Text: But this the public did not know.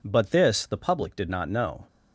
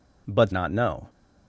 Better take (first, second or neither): first